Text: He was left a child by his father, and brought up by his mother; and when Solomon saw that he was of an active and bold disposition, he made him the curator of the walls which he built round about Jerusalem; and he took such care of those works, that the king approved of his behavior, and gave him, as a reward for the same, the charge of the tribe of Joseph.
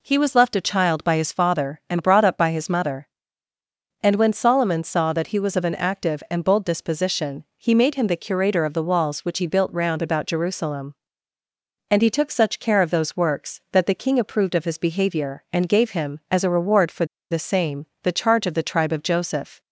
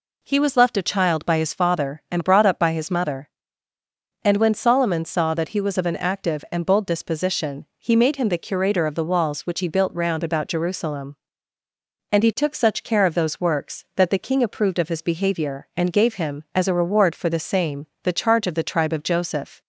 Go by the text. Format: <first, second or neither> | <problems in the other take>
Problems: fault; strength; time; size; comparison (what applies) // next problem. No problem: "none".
second | pauses between "for" and "the"; slight; at 17.0 s; 0.25 s long